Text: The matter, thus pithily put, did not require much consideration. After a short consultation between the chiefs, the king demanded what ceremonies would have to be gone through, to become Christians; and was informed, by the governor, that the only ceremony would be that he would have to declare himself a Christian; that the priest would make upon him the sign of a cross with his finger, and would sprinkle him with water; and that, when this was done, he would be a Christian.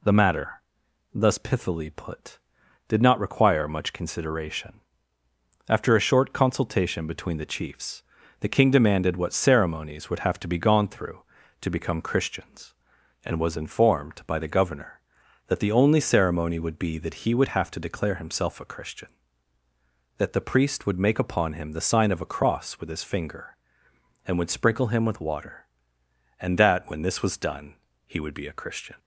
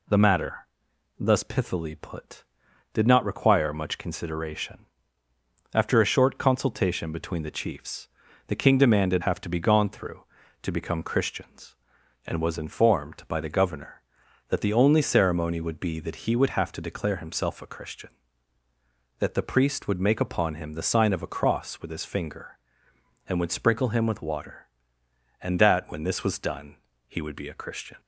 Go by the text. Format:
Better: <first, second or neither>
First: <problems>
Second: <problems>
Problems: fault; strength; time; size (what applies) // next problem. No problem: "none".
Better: first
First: none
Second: skips "what ceremonies would"; at 9.2 s